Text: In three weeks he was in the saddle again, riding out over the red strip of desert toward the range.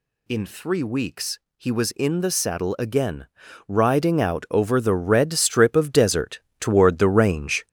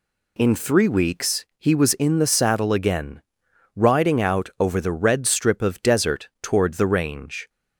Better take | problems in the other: second | gets louder; throughout; 6.5 dB // pauses between "weeks" and "he"; slight; at 1.3 s; 0.16 s long // pauses between "desert" and "toward"; slight; at 6.3 s; 0.20 s long

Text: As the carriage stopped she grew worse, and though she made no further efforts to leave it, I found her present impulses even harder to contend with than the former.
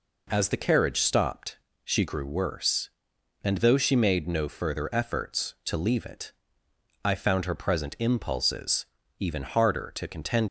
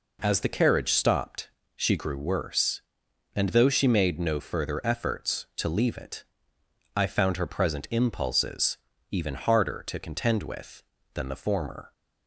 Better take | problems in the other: second | pauses between "stopped" and "she"; slight; at 1.5 s; 0.28 s long; slight in the second // pauses between "impulses" and "even"; slight; at 8.8 s; 0.34 s long; slight in the second // stops before "with than the former"; at 10.4 s

